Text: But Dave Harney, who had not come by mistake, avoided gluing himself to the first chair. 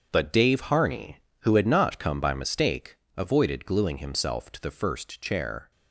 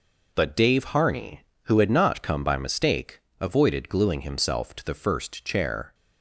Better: second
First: gets quieter; strong; throughout; 10.5 dB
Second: none

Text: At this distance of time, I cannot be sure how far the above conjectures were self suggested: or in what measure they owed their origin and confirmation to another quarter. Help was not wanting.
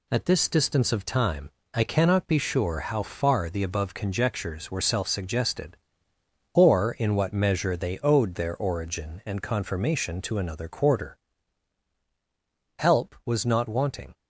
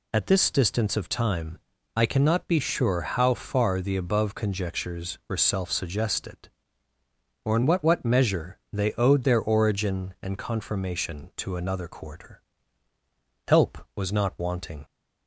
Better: first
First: none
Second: says "what" twice; at 7.8 s

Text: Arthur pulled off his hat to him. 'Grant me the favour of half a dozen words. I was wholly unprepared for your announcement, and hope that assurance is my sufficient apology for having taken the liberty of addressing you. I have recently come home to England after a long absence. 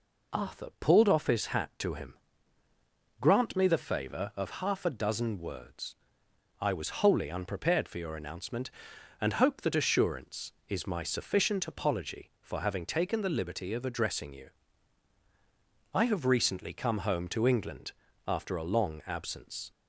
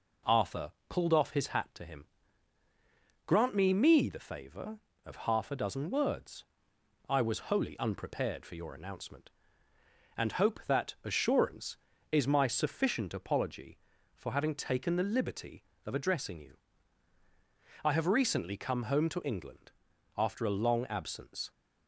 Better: first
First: pauses between "England" and "after"; slight; at 17.9 s; 0.36 s long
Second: pauses between "Arthur" and "pulled"; slight; at 0.7 s; 0.16 s long // says "me" twice; at 3.7 s // pauses between "England" and "after"; at 19.7 s; 0.44 s long

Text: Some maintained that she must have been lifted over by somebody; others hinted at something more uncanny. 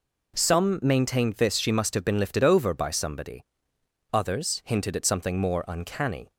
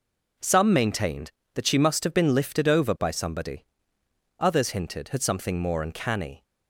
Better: second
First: says "this" for "that"; at 1.3 s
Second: none

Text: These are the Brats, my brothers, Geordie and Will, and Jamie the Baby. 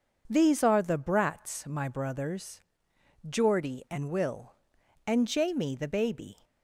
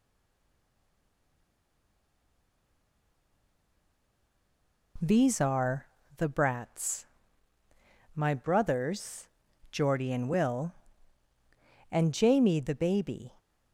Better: first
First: none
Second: stays silent before the first word; strong; until 4.9 s; 4.9 s long // pauses between "are" and "the"; slight; at 5.8 s; 0.30 s long

